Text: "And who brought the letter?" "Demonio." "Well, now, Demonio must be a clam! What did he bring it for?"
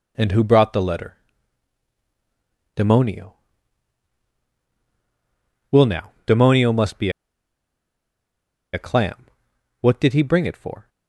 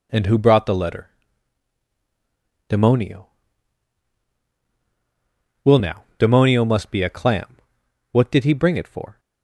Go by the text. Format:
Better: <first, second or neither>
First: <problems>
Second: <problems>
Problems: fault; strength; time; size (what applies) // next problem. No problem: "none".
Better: second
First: pauses between "be" and "a"; strong; at 7.0 s; 1.6 s long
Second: none